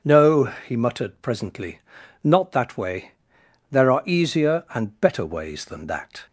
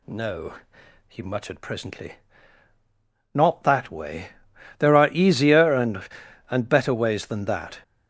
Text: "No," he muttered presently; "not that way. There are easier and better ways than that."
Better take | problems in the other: first | says "and" twice; at 6.5 s

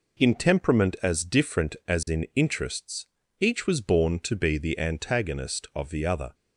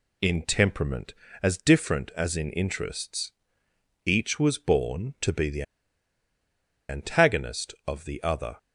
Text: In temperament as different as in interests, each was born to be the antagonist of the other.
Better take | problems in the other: first | pauses between "the" and "antagonist"; strong; at 5.6 s; 1.2 s long

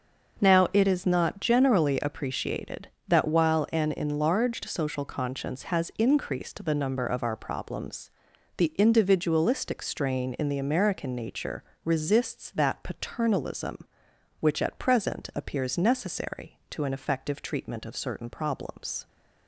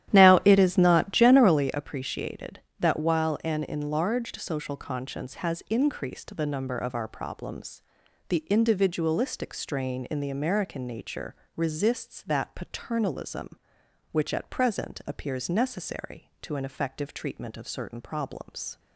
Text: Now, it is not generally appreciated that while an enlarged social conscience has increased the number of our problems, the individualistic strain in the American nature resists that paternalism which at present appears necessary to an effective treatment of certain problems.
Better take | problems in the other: first | starts louder than the rest; strong; until 1.7 s; 11.5 dB // pauses between "nature" and "resists"; slight; at 11.3 s; 0.20 s long; slight in the first

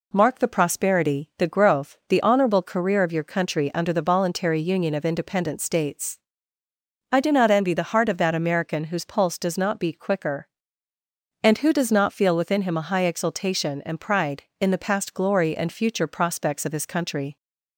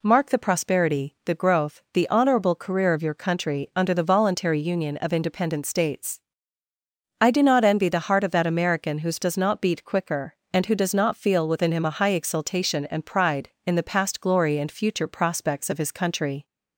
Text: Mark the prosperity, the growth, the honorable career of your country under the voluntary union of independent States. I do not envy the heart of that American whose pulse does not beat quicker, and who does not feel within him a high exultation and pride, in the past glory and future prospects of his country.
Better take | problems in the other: first | skips "pulse"; at 9.1 s

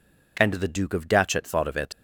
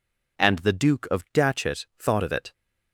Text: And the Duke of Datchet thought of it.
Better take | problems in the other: second | leaves "it" unfinished; at 1.9 s; 85 ms

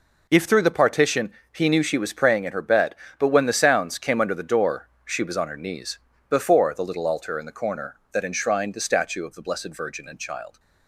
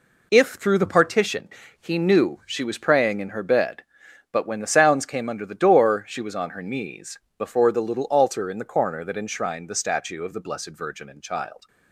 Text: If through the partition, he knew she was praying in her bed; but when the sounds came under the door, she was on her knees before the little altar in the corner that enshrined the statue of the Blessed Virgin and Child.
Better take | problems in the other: neither | pauses between "knees" and "before"; slight; the same in both

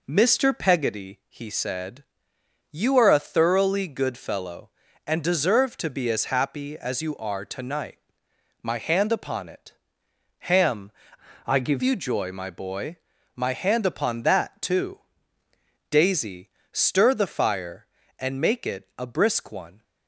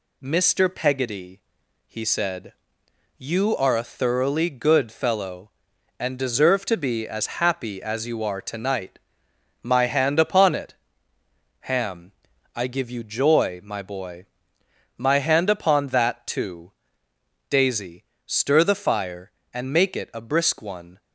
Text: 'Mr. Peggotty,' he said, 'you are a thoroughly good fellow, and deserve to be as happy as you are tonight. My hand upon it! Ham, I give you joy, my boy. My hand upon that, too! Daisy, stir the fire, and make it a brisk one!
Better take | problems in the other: second | changes voice from "I" to "give"; from 11.4 to 11.8 s; 0.4 s long

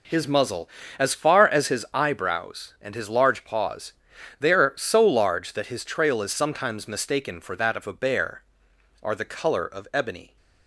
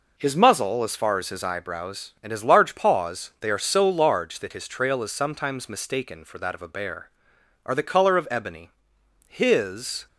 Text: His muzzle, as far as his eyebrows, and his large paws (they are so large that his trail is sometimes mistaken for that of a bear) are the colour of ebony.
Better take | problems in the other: first | goes on to say "His"; noticeable; from 9.2 s on; 0.80 s long

